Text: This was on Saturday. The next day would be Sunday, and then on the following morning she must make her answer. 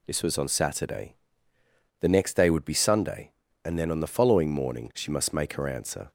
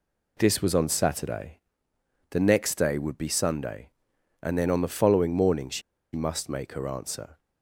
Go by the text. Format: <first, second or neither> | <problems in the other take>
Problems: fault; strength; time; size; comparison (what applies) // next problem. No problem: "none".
first | pauses between "she" and "must"; slight; at 5.8 s; 0.33 s long